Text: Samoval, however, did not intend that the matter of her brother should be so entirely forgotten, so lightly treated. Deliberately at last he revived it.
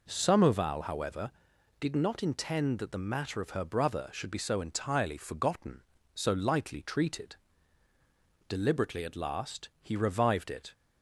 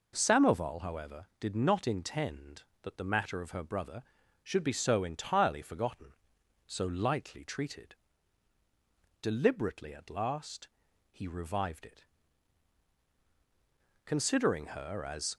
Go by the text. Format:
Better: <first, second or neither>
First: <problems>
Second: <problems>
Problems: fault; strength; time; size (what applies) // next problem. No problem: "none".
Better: first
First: none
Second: pauses between "last" and "he"; at 10.6 s; 0.42 s long // goes on to say "Considering her as"; noticeable; from 14.0 s on; 1.3 s long